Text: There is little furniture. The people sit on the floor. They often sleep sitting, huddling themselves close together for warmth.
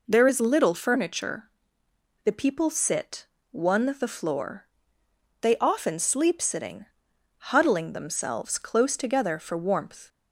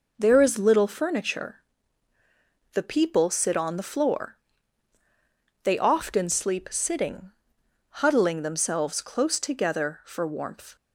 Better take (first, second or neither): second